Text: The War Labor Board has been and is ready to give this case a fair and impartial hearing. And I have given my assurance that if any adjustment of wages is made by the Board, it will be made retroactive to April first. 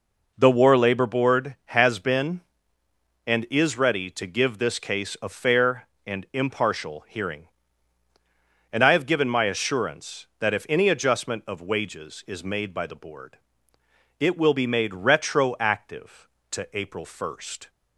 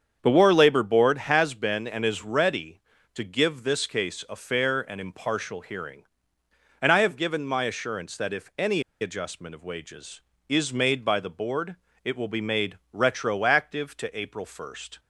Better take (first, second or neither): first